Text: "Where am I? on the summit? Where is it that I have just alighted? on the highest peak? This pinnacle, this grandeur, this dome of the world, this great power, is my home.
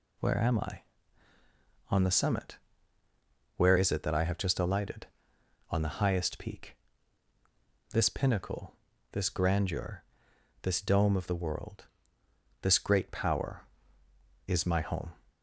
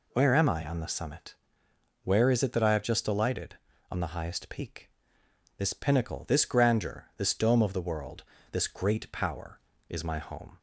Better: neither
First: none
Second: none

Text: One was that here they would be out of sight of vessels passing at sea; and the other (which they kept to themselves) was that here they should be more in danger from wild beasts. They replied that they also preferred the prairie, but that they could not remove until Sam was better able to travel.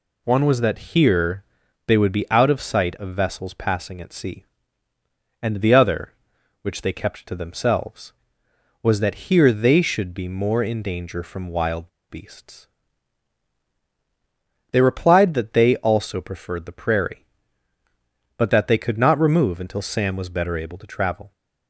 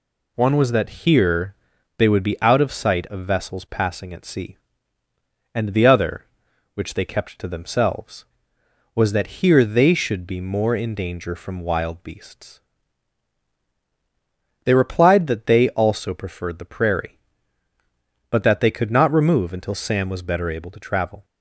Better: second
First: pauses between "here" and "they"; at 1.4 s; 0.42 s long // pauses between "wild" and "beasts"; slight; at 11.8 s; 0.19 s long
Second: pauses between "here" and "they"; at 1.5 s; 0.42 s long

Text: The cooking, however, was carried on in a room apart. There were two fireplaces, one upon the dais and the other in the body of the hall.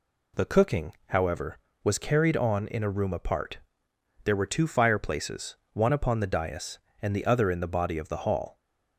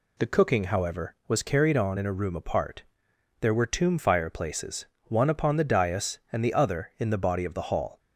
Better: first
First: none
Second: says "tomb" for "two"; at 3.6 s

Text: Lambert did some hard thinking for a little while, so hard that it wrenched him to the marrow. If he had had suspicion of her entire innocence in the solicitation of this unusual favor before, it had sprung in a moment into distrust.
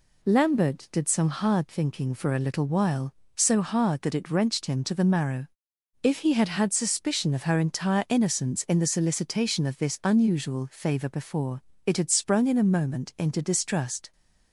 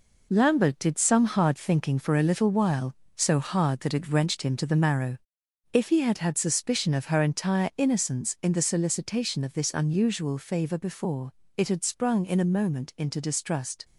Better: first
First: none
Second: gets quieter; throughout; 6.5 dB

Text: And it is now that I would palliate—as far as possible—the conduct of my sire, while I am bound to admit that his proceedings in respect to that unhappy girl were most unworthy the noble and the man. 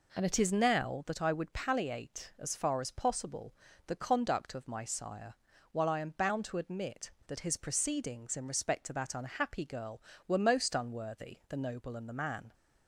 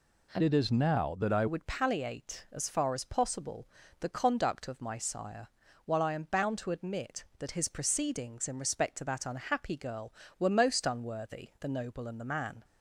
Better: first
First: none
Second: changes voice from "it" to "I"; from 0.4 to 1.4 s; 1.0 s long

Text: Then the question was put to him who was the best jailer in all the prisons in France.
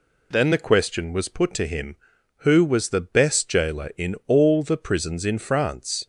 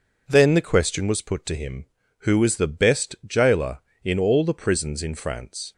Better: neither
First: none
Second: none

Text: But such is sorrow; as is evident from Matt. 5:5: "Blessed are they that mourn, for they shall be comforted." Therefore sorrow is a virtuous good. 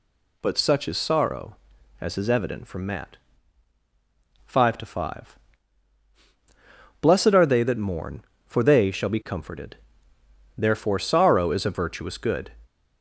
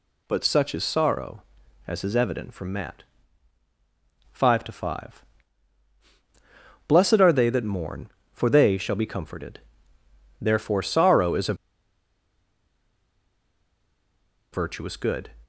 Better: first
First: none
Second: pauses between "a" and "virtuous"; strong; at 11.5 s; 2.9 s long

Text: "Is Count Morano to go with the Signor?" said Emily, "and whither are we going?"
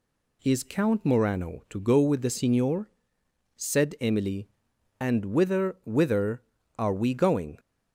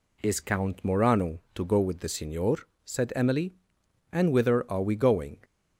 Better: second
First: says "whither" twice; at 5.8 s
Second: none

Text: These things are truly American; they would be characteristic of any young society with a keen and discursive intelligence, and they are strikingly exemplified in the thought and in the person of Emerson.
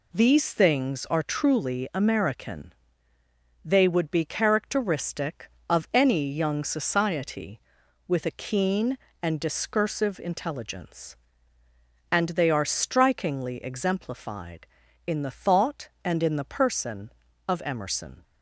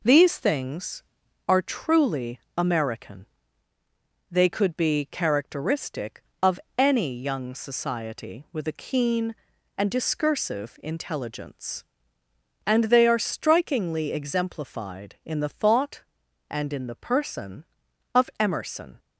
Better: first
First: none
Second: pauses between "truly" and "American"; slight; at 2.4 s; 0.16 s long // says "could" for "would"; at 4.4 s // pauses between "of" and "any"; slight; at 6.5 s; 0.18 s long

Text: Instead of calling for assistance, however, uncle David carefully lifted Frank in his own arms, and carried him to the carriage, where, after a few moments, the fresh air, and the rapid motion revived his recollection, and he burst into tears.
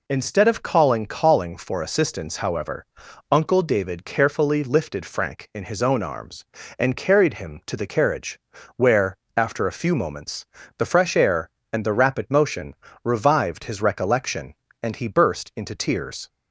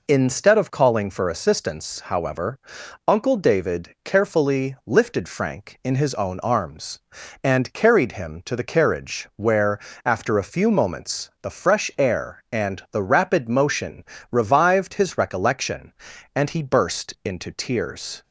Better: second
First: says "calling" twice; at 1.0 s // pauses between "motion" and "revived"; slight; at 12.7 s; 0.30 s long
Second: pauses between "motion" and "revived"; slight; at 14.0 s; 0.26 s long

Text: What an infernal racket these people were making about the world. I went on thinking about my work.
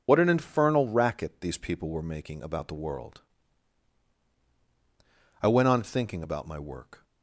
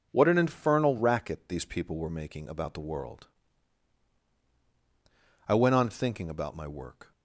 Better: second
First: loses the start of "What"; at 0.0 s; 70 ms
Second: none

